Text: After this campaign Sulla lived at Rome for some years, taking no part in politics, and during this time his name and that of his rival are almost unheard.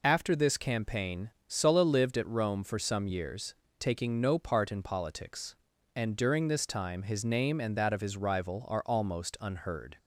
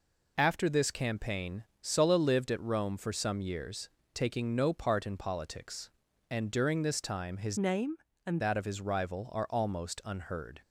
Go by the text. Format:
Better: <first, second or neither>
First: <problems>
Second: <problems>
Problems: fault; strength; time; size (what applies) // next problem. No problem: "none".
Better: first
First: pauses between "campaign" and "Sulla"; slight; at 1.3 s; 0.18 s long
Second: pauses between "campaign" and "Sulla"; slight; at 1.6 s; 0.18 s long // changes voice from "name" to "and"; from 7.5 to 8.4 s; 0.9 s long